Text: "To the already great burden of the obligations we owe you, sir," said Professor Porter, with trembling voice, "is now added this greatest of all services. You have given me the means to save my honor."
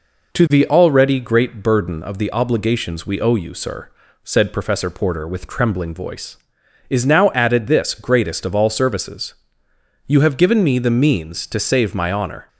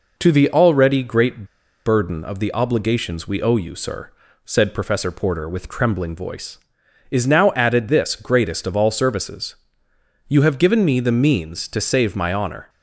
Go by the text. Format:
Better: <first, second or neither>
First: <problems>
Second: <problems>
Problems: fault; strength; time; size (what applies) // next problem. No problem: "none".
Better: first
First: none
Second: pauses between "great" and "burden"; at 1.4 s; 0.40 s long